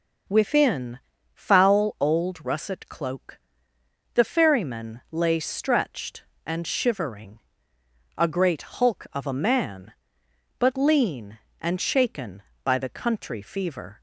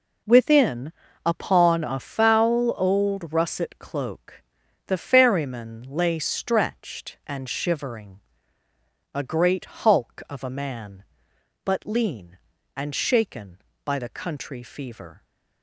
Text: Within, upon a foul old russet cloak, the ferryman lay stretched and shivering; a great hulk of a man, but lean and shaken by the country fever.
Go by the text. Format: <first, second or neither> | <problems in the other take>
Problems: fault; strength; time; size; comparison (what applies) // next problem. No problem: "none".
second | skips "upon a"; at 1.1 s